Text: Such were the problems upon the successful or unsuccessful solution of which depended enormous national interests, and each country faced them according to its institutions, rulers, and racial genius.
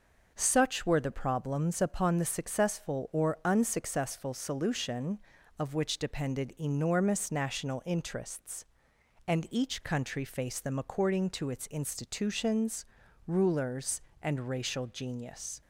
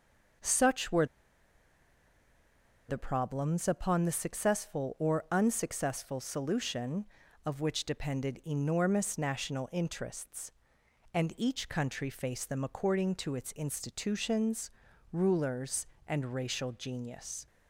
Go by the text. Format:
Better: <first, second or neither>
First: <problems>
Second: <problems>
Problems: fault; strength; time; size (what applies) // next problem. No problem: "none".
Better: first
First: none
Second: pauses between "were" and "the"; strong; at 1.0 s; 1.8 s long